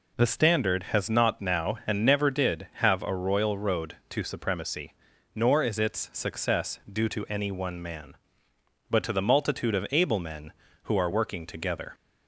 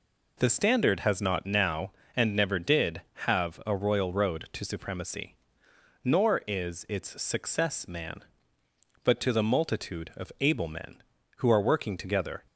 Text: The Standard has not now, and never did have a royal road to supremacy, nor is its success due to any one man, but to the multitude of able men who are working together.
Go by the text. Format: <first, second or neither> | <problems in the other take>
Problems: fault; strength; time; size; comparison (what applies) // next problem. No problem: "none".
first | skips "due to any one"; at 7.8 s